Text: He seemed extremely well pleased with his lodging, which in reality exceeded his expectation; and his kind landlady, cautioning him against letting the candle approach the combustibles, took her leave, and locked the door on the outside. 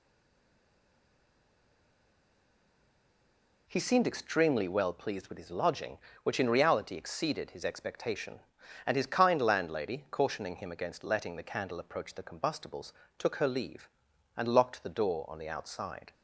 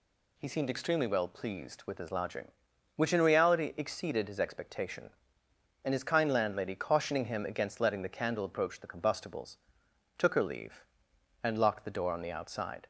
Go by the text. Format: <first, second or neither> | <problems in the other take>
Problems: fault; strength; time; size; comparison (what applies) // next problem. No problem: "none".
second | stays silent before the first word; strong; until 3.6 s; 3.6 s long